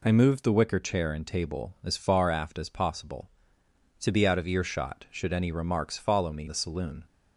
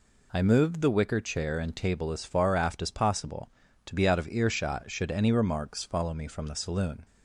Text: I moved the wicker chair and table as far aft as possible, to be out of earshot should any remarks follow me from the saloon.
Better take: second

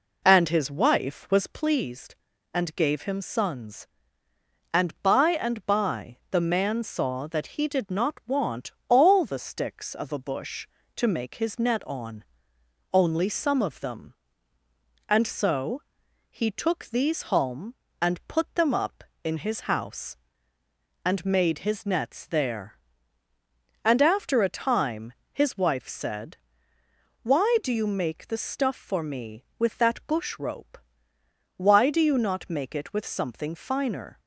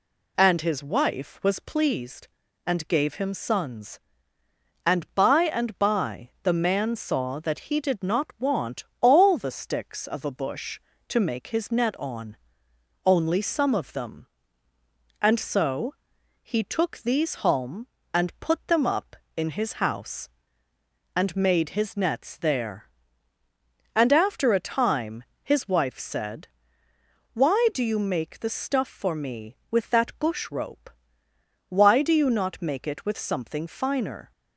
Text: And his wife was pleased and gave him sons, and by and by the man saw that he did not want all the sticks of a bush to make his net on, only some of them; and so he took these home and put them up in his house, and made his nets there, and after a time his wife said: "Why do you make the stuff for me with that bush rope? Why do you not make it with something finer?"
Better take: second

